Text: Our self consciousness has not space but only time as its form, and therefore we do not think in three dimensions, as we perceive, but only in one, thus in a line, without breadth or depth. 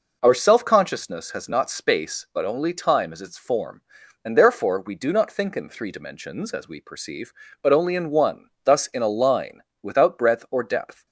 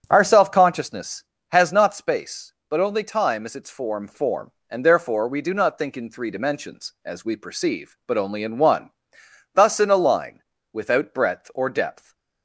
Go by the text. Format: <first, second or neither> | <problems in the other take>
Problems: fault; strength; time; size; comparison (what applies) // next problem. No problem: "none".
first | starts louder than the rest; strong; until 1.1 s; 7 dB // says "form" twice; at 4.0 s